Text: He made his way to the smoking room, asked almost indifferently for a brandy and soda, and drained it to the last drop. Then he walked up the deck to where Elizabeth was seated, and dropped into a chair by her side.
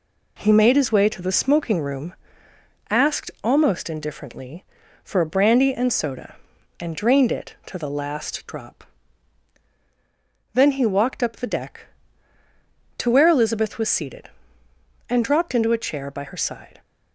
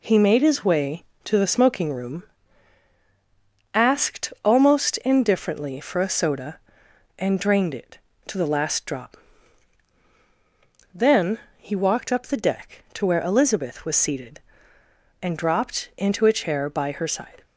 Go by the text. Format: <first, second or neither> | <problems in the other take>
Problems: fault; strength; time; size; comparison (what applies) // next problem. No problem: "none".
first | skips "brandy and"; at 6.0 s // pauses between "Then" and "he"; slight; at 11.3 s; 0.18 s long